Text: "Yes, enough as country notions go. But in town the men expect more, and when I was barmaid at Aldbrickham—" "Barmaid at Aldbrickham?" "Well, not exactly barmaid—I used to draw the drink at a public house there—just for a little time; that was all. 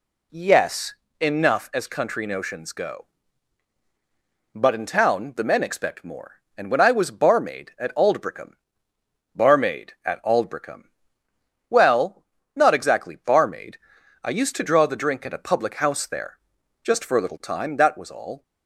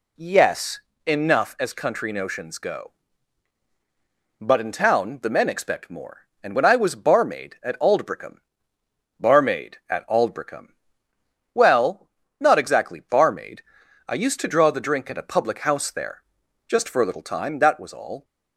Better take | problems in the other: neither | none

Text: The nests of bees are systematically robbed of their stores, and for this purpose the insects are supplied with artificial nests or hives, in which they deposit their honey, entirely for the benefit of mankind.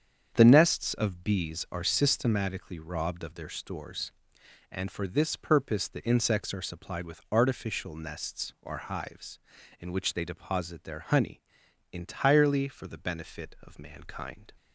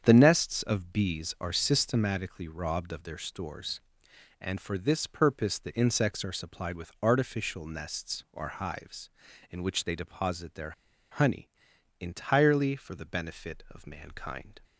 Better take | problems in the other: first | starts louder than the rest; strong; until 1.0 s; 7.5 dB; strong in the first // pauses between "their" and "honey"; at 10.7 s; 0.40 s long

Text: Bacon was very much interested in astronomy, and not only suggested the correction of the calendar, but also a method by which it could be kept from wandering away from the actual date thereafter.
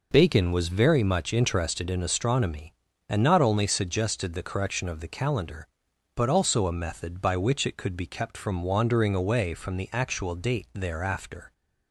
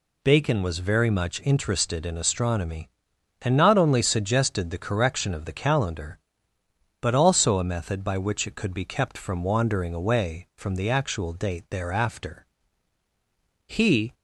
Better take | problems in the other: first | goes on to say "He"; slight; from 13.6 s on; 0.48 s long

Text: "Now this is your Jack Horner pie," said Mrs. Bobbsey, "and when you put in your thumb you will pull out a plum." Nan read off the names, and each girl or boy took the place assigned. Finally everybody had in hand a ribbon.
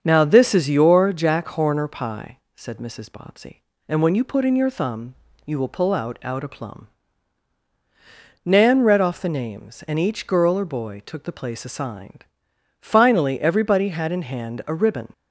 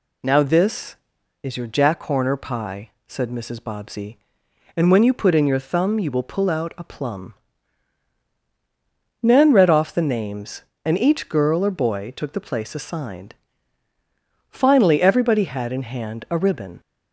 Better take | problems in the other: second | starts louder than the rest; until 1.0 s; 7 dB // pauses between "thumb" and "you"; slight; at 5.1 s; 0.30 s long // says "out" twice; at 6.2 s

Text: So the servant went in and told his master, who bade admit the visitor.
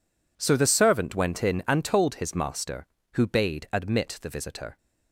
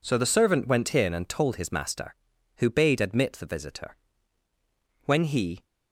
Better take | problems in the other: first | goes on to say "When he"; from 5.0 s on; 0.58 s long

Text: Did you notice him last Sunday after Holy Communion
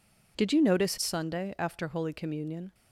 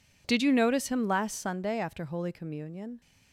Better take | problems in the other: second | skips "him last"; at 0.9 s

